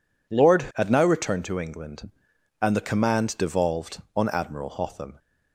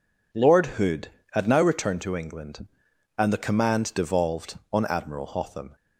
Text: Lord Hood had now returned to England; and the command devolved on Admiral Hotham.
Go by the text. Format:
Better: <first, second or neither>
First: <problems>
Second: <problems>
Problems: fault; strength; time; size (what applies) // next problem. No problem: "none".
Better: second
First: skips "Hood"; at 0.7 s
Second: none